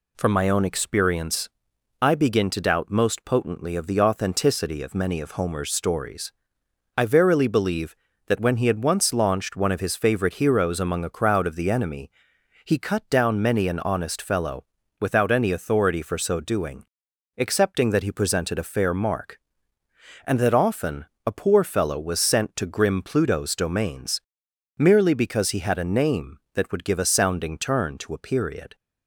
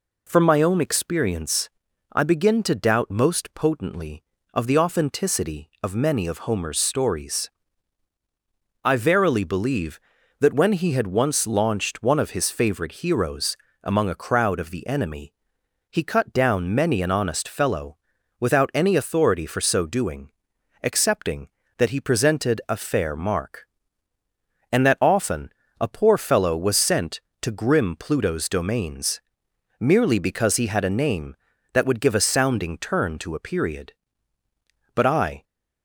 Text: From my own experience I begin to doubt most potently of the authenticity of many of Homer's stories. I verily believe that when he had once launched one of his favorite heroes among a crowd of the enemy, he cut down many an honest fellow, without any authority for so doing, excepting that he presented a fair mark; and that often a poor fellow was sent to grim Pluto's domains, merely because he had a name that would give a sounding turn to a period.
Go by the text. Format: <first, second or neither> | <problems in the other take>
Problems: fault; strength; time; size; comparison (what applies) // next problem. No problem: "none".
first | pauses between "experience" and "I"; at 1.6 s; 0.42 s long; noticeable in the first // pauses between "heroes" and "among"; slight; at 13.5 s; 0.26 s long // pauses between "often" and "a"; slight; at 25.4 s; 0.32 s long; slight in the first // goes on to say "But I"; slight; from 34.9 s on; 0.48 s long